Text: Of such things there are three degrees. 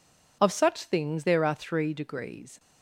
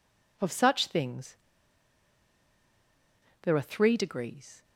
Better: first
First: none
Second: pauses between "things" and "there"; strong; at 1.3 s; 2.0 s long

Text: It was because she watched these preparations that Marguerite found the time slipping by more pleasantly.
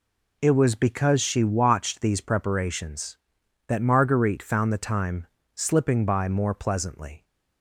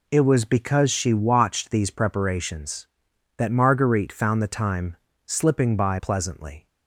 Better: first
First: pauses between "time" and "slipping"; slight; at 5.2 s; 0.28 s long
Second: pauses between "time" and "slipping"; slight; at 4.9 s; 0.30 s long // skips "more"; at 5.9 s

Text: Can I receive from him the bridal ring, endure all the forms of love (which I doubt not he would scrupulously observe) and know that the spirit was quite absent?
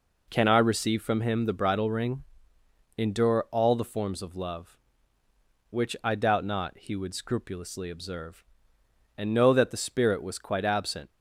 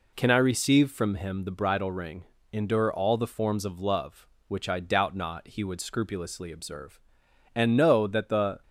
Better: first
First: none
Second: stops before "spirit was quite absent"; at 8.6 s

